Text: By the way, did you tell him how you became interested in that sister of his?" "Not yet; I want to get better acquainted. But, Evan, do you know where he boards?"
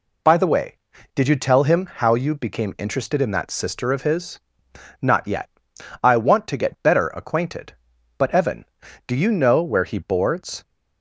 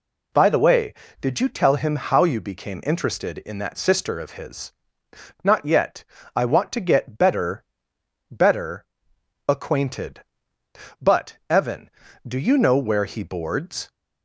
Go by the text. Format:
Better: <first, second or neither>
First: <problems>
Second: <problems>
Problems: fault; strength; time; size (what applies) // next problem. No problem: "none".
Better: first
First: none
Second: says "better" twice; at 8.3 s